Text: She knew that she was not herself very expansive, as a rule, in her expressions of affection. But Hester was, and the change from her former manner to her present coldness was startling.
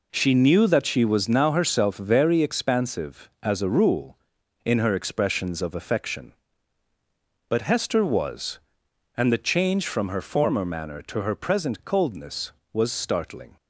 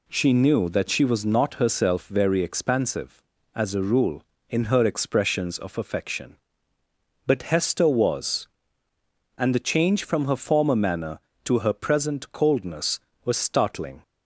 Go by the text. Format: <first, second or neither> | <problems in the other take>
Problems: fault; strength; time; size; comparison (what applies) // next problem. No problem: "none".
second | says "now" for "not"; at 1.2 s